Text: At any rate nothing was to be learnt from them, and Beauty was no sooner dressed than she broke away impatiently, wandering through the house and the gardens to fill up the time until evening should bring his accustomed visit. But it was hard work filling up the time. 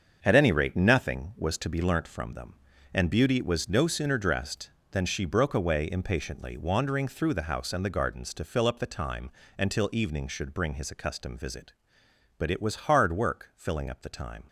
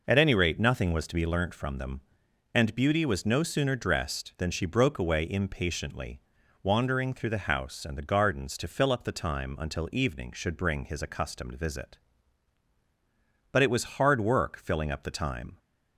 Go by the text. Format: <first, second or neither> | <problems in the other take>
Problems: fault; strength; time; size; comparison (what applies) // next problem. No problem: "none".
second | gets quieter; strong; throughout; 9 dB // pauses between "time" and "until"; slight; at 9.3 s; 0.26 s long